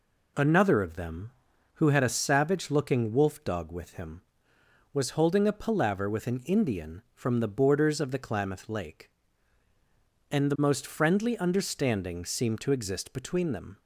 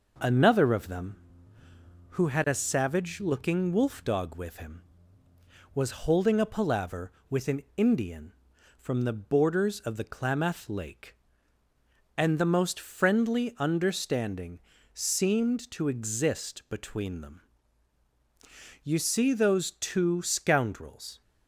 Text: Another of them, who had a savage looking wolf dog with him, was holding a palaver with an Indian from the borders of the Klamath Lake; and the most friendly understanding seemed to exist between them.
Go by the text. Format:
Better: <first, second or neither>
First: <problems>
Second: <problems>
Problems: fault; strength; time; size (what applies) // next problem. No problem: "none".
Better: first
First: none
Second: pauses between "understanding" and "seemed"; slight; at 14.5 s; 0.34 s long // goes on to say "You see those two scoundrels"; strong; from 18.8 s on; 2.3 s long